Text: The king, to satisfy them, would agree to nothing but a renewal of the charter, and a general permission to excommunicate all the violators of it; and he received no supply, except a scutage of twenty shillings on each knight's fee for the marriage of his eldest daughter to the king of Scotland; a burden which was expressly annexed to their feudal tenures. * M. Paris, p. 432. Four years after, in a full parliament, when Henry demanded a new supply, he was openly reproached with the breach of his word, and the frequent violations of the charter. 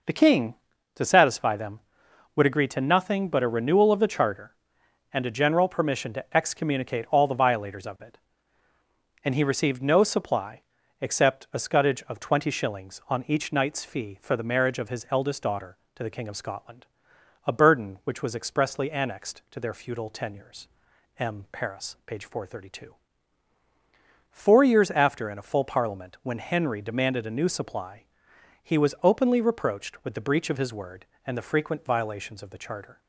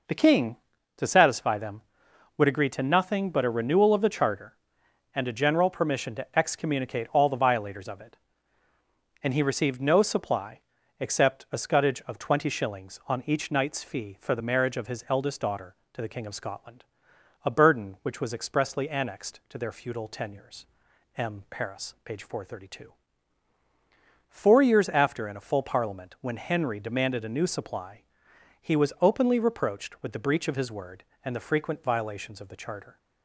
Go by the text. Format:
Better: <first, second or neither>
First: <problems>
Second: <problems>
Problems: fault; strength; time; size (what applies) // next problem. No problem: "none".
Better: neither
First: none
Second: none